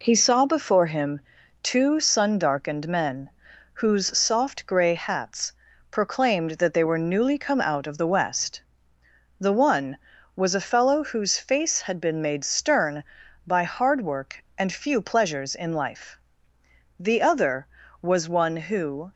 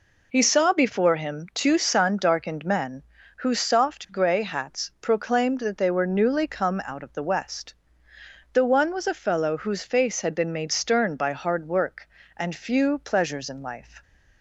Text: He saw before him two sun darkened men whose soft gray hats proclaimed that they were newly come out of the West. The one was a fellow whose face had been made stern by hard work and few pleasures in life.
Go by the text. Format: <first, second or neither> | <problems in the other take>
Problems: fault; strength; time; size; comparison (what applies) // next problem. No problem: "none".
second | pauses between "him" and "two"; at 1.1 s; 0.42 s long // pauses between "men" and "whose"; at 3.2 s; 0.44 s long; slight in the second // pauses between "hats" and "proclaimed"; at 5.5 s; 0.40 s long // goes on to say "The other was one who"; strong; from 16.9 s on; 2.1 s long